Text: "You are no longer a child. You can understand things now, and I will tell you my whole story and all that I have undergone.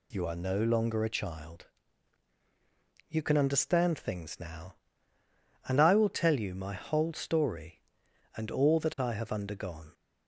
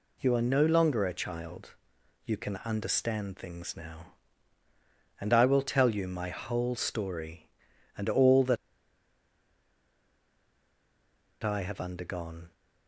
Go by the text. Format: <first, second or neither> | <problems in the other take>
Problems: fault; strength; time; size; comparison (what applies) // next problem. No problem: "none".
first | pauses between "that" and "I"; strong; at 8.5 s; 2.8 s long